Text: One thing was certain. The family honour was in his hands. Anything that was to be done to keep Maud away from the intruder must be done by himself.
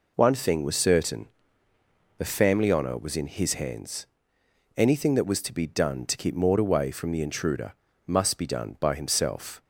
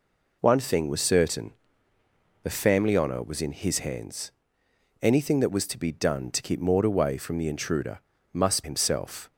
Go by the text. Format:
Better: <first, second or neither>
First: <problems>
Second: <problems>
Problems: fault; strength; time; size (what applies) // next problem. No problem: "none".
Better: first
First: pauses between "intruder" and "must"; slight; at 7.7 s; 0.32 s long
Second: pauses between "intruder" and "must"; slight; at 7.9 s; 0.32 s long // skips "be done by"; at 8.6 s